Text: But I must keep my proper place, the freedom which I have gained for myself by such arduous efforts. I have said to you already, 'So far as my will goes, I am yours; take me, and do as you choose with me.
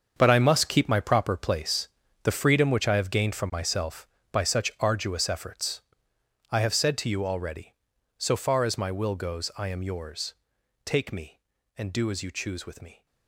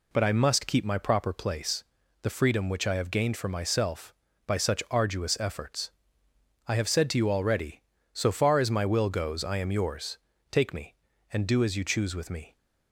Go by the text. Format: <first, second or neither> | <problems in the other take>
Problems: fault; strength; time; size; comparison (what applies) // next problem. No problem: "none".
second | gets quieter; strong; throughout; 13 dB